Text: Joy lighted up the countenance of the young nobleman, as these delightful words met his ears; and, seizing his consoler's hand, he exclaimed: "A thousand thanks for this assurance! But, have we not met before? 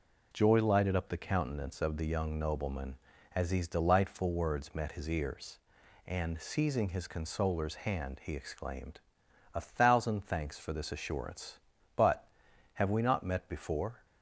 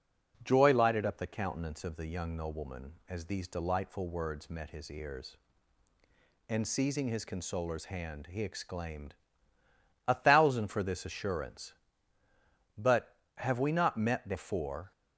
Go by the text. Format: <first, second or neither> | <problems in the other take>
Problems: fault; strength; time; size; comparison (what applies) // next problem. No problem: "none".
first | skips "thanks"; at 10.6 s